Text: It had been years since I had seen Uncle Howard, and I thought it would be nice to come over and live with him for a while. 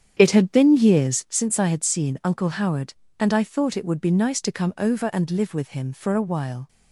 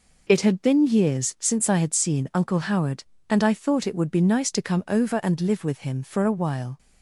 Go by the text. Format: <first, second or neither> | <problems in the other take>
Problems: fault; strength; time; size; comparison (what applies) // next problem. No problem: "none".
second | starts louder than the rest; strong; until 1.4 s; 8.5 dB